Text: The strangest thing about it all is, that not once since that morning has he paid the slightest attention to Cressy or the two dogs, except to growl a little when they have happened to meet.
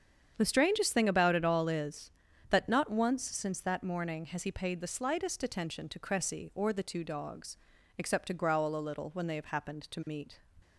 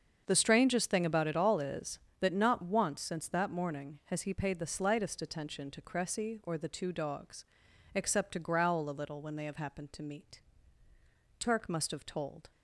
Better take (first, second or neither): first